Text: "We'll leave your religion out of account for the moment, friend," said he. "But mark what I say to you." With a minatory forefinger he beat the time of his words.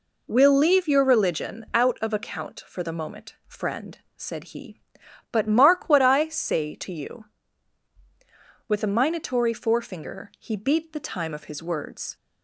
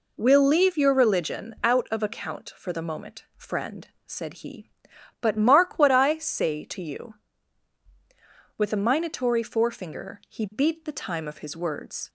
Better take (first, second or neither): neither